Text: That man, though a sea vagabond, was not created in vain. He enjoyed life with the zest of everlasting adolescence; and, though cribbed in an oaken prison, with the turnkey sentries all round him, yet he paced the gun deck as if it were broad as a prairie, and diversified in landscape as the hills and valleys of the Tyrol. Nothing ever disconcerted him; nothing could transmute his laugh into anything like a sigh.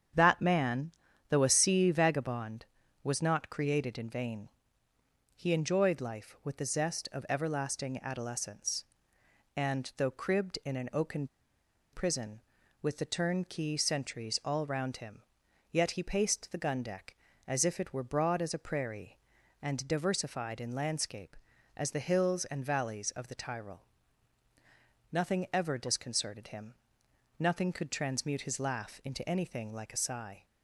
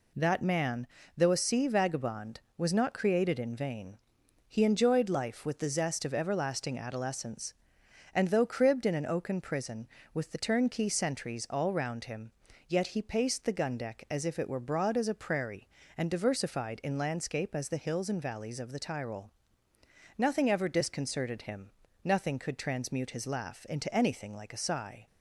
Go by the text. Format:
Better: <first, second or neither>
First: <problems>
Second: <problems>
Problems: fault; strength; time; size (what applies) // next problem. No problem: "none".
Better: second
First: starts louder than the rest; strong; until 1.5 s; 8 dB // pauses between "oaken" and "prison"; noticeable; at 11.2 s; 0.66 s long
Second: none